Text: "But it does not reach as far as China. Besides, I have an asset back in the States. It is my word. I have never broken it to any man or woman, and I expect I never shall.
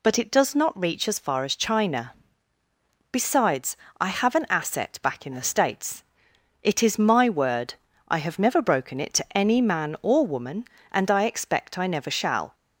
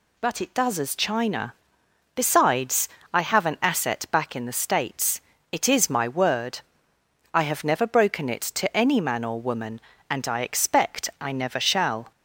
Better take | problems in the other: first | skips "not reach as far"; at 0.7 s

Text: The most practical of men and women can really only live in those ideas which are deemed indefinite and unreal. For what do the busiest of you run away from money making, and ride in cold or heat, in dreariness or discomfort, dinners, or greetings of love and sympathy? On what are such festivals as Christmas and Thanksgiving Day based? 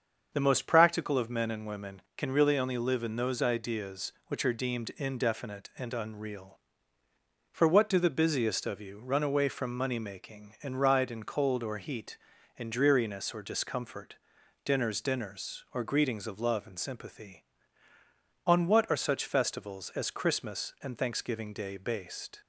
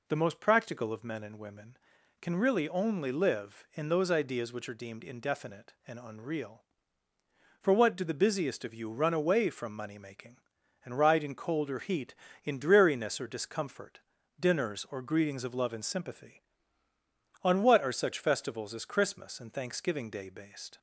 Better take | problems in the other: second | starts louder than the rest; until 1.3 s; 7 dB // says "dinners" twice; at 15.0 s

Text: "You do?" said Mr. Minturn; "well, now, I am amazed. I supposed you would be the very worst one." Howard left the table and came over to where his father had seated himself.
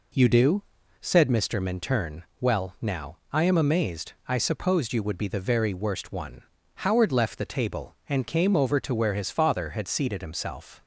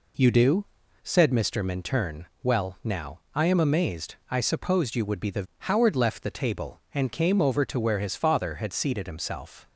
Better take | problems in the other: first | skips "very worst one"; at 5.5 s

